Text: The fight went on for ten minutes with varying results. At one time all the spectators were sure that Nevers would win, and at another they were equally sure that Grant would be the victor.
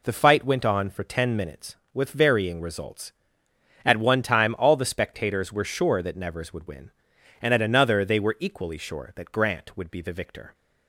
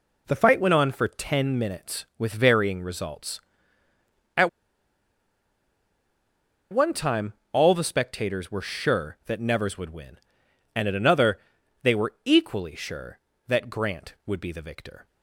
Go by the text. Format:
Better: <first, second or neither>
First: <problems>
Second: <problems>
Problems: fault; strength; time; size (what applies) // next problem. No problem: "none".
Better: first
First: none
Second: pauses between "At" and "one"; strong; at 4.4 s; 2.2 s long // pauses between "time" and "all"; slight; at 7.3 s; 0.20 s long // pauses between "another" and "they"; at 11.3 s; 0.42 s long